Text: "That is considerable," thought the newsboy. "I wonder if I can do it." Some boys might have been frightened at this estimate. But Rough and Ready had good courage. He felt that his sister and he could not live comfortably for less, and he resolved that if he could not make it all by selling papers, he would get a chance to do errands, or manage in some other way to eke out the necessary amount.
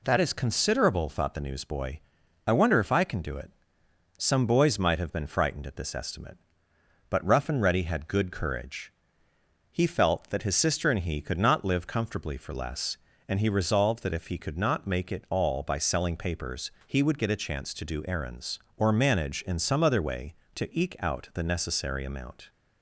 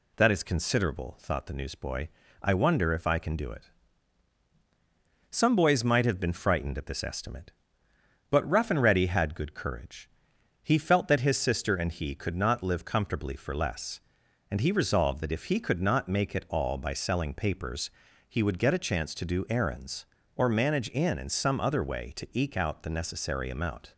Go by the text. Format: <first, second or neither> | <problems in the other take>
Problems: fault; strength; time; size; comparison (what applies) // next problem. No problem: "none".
first | says "in" twice; at 21.1 s